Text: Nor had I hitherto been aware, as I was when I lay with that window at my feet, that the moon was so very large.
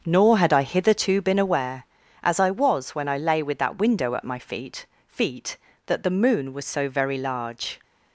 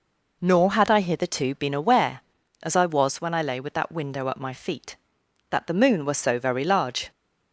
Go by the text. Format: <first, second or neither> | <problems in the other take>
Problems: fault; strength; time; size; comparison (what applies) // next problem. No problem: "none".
second | starts louder than the rest; until 1.0 s; 7 dB // says "feet" twice; at 5.0 s